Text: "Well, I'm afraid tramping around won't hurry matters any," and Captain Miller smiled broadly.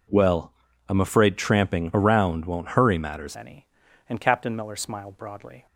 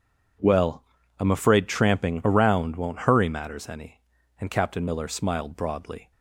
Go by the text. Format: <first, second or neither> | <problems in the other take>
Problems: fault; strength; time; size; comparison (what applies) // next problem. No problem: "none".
second | changes voice at "any"; from 3.3 s on; 2.3 s long